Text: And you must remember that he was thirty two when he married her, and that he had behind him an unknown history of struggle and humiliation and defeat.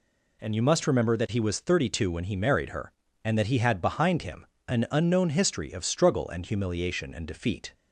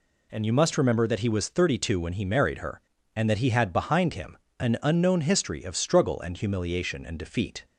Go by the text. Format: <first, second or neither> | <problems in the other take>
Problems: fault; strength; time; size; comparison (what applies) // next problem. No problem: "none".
neither | pauses between "him" and "an"; slight; the same in both